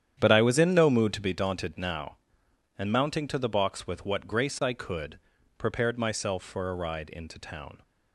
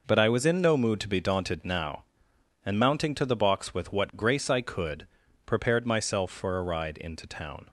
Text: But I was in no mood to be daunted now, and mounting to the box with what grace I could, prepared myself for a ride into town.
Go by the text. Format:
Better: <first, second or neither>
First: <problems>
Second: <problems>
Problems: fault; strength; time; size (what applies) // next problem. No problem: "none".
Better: second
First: starts louder than the rest; strong; until 1.3 s; 9.5 dB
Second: none